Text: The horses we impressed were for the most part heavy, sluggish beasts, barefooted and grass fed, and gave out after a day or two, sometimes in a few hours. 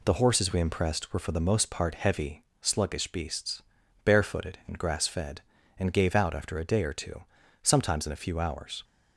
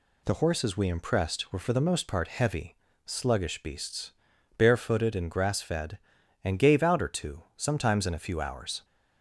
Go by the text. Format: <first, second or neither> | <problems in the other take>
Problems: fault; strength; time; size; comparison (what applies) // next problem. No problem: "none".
first | skips "after a day"; at 7.0 s